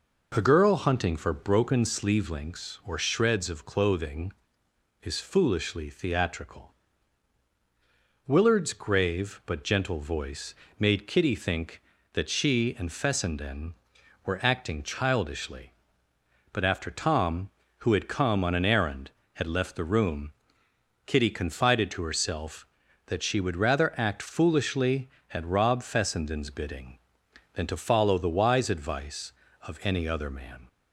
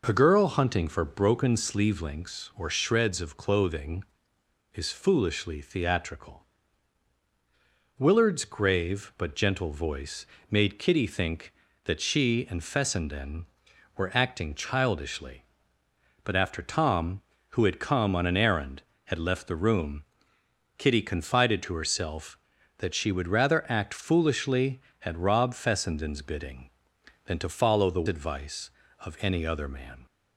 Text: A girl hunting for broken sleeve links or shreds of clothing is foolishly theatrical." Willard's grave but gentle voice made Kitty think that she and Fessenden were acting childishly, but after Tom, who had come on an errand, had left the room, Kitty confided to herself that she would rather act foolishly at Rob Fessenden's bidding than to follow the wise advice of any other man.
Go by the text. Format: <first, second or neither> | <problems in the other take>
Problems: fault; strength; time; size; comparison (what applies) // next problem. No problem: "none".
first | pauses between "voice" and "made"; slight; at 10.2 s; 0.24 s long; slight in the first // skips "wise"; at 28.0 s